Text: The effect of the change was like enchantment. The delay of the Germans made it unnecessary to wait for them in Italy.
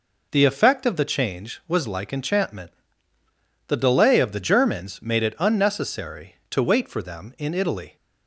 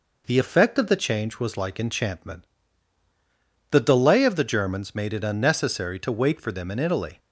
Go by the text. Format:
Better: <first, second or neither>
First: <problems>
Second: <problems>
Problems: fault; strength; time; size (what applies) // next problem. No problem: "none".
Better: neither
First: none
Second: none